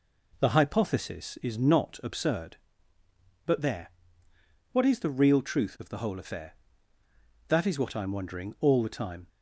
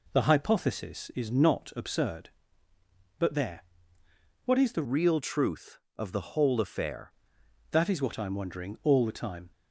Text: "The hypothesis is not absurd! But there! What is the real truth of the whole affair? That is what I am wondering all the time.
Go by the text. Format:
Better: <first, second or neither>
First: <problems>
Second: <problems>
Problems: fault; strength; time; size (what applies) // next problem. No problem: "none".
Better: first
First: none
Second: changes voice from "real" to "affair"; from 4.8 to 7.1 s; 2.3 s long